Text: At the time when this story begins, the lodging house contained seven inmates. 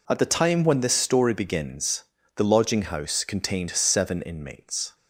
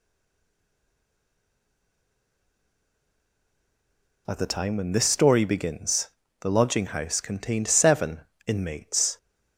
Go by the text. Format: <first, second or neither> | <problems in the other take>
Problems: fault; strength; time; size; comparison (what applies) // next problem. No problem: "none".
first | stays silent before the first word; strong; until 4.2 s; 4.2 s long // pauses between "seven" and "inmates"; slight; at 8.2 s; 0.26 s long